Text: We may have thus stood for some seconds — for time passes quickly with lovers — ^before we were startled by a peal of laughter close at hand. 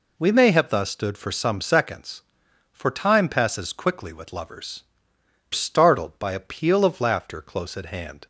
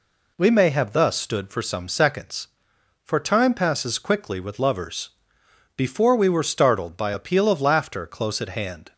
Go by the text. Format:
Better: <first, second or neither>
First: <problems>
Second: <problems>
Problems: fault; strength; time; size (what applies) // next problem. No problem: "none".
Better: second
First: skips "before we were"; at 5.1 s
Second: none